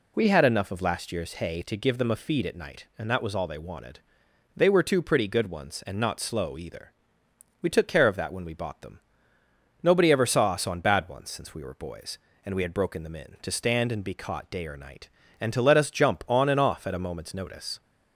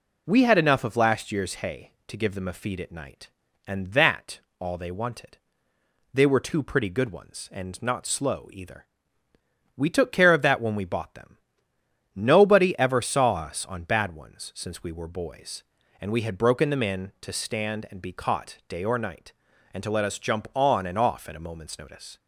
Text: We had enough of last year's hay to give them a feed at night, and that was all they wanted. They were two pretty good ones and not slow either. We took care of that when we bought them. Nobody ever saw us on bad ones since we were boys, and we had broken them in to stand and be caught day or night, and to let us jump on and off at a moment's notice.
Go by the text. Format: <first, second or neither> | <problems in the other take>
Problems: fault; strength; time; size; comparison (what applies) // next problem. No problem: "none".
first | skips "was"; at 4.4 s